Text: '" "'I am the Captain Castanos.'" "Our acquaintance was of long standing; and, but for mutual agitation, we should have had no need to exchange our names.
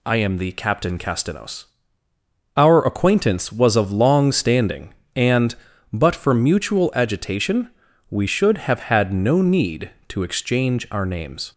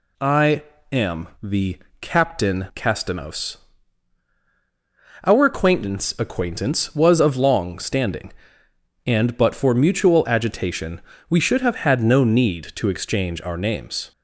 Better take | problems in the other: first | pauses between "I" and "am"; slight; at 0.6 s; 0.30 s long // pauses between "the" and "Captain"; slight; at 1.7 s; 0.24 s long // says "acquaintance" twice; at 6.1 s

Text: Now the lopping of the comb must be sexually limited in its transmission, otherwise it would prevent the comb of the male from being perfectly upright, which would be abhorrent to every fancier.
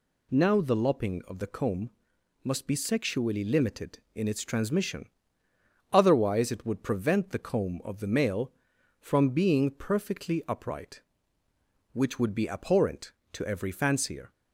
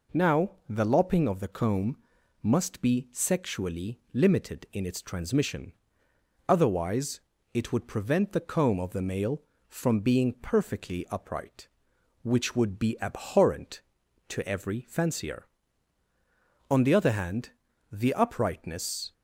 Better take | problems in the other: first | pauses between "Now" and "the"; slight; at 0.5 s; 0.18 s long // pauses between "comb" and "must"; noticeable; at 1.9 s; 0.46 s long; noticeable in the first // pauses between "otherwise" and "it"; slight; at 7.2 s; 0.34 s long // goes on to say "On the other hand the uprightness"; strong; from 16.7 s on; 2.4 s long

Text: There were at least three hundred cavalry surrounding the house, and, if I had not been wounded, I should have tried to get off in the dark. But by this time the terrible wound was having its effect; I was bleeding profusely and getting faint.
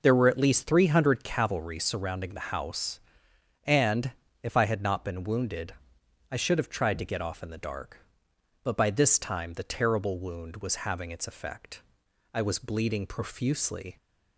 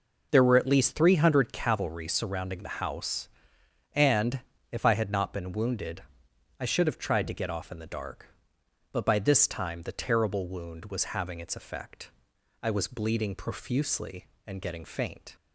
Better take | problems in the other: second | stops before "and getting faint"; at 13.9 s

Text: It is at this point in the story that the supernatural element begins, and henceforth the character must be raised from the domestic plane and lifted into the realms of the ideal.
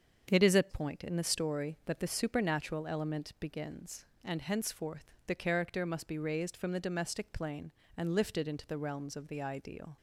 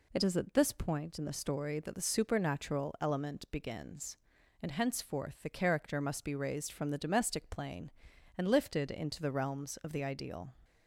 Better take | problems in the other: second | starts louder than the rest; strong; until 1.3 s; 7 dB // skips "this"; at 0.6 s

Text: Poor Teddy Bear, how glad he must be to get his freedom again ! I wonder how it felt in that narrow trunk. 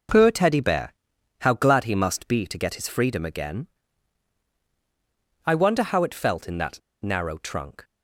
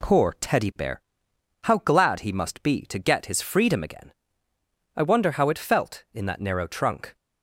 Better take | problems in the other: second | pauses between "that" and "narrow"; slight; at 6.8 s; 0.23 s long

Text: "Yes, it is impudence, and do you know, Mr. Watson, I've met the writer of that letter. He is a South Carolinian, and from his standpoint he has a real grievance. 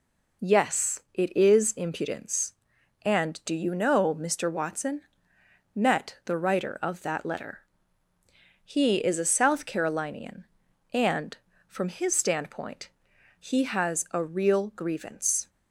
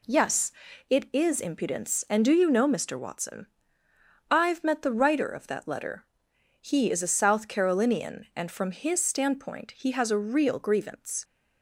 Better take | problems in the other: second | skips "I've"; at 5.3 s // pauses between "standpoint" and "he"; noticeable; at 12.8 s; 0.50 s long

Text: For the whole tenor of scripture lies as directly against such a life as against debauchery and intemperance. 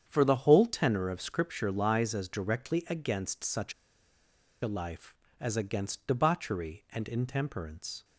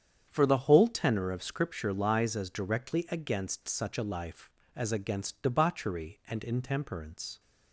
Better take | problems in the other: second | starts louder than the rest; strong; until 1.0 s; 8.5 dB; strong in the second // pauses between "such" and "a"; noticeable; at 3.7 s; 0.89 s long

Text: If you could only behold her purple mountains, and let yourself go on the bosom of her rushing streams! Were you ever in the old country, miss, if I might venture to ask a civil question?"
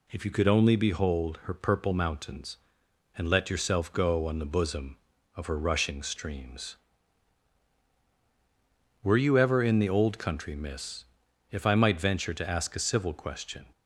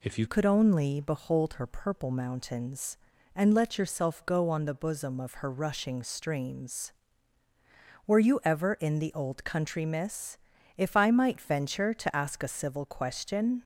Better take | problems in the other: first | changes voice at "could"; from 0.2 s on; 13.4 s long

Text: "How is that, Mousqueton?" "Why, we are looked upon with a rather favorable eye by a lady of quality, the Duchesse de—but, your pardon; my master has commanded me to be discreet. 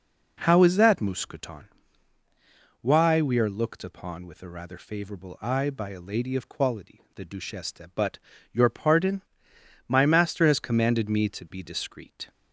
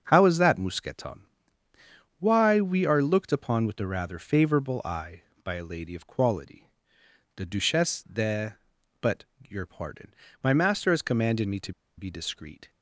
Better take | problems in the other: first | starts louder than the rest; until 1.0 s; 6.5 dB // pauses between "to" and "be"; slight; at 11.7 s; 0.25 s long

